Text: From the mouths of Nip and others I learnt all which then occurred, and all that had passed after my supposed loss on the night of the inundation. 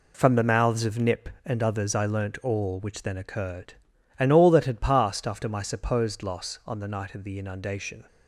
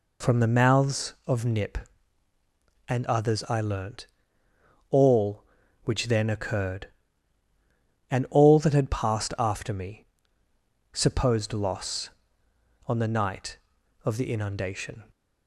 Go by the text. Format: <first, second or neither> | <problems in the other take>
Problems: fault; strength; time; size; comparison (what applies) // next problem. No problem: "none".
first | pauses between "learnt" and "all"; noticeable; at 4.0 s; 0.86 s long // says "me" for "my"; at 9.7 s